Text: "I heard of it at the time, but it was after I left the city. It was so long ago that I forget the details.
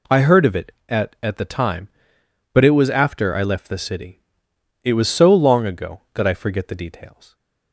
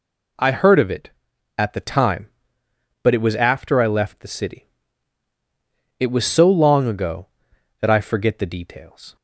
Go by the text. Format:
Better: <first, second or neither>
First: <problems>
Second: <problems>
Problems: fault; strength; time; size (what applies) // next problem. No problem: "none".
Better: second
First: says "at" twice; at 1.2 s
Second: none